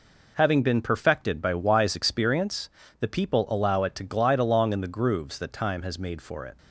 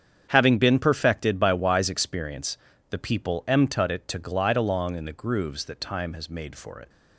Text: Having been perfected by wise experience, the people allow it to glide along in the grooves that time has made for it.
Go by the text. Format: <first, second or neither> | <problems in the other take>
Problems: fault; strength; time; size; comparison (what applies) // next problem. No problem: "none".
first | starts louder than the rest; strong; until 1.3 s; 8.5 dB // says "mtut" for "allow"; at 3.4 s